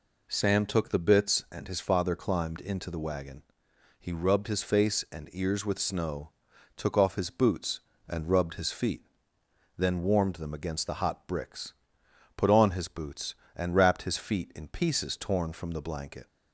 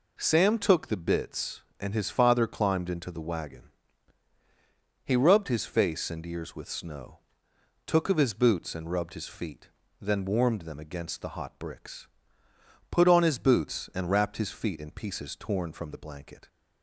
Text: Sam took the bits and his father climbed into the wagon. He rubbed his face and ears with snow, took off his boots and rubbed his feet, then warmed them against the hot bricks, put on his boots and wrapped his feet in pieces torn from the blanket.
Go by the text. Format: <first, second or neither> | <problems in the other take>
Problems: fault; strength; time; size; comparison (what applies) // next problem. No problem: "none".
first | says "of" for "off"; at 8.0 s